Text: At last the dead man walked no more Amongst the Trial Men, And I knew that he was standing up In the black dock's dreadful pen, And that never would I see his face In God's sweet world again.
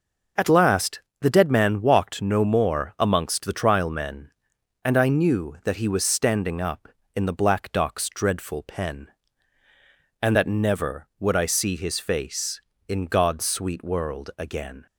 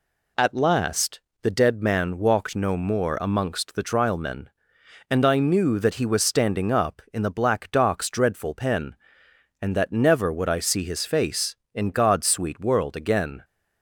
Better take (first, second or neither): neither